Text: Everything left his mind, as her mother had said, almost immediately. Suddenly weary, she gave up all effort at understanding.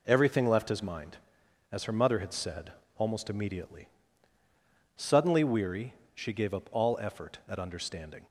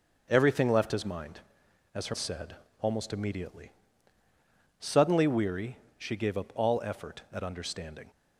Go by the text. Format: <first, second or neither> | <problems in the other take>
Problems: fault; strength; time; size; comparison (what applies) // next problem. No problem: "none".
first | starts louder than the rest; noticeable; until 1.3 s; 6 dB // skips "mother had"; at 2.1 s